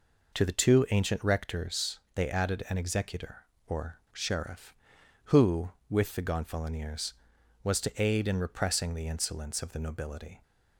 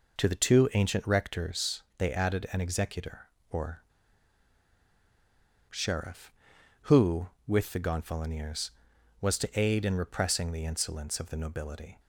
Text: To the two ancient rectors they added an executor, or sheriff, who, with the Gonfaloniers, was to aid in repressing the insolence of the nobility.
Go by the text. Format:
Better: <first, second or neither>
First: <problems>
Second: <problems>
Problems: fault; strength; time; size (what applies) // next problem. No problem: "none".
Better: first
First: pauses between "rectors" and "they"; slight; at 1.9 s; 0.16 s long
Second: pauses between "rectors" and "they"; slight; at 1.8 s; 0.16 s long // pauses between "or" and "sheriff"; strong; at 3.8 s; 1.8 s long